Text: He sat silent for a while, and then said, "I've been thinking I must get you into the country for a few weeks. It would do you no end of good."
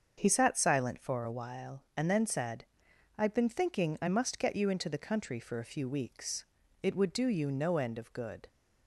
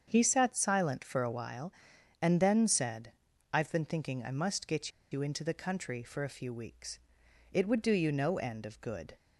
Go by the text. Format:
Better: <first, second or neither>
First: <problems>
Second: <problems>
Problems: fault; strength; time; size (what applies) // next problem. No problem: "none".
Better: first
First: starts louder than the rest; until 1.1 s; 7 dB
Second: starts louder than the rest; strong; until 1.0 s; 7.5 dB // pauses between "get" and "you"; slight; at 4.9 s; 0.20 s long